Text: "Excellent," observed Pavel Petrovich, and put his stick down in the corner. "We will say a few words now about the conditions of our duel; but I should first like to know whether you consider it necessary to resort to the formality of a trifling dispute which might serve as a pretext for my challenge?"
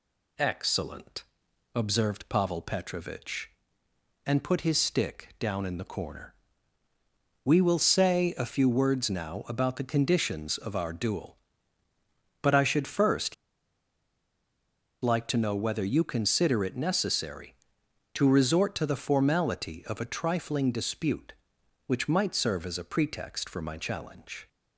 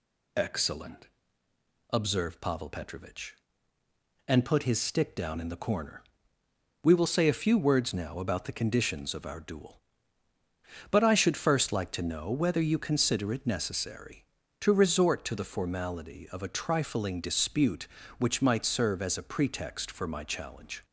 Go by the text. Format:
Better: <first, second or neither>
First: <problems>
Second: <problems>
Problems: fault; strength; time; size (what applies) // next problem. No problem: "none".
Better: second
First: pauses between "first" and "like"; strong; at 13.3 s; 1.6 s long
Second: none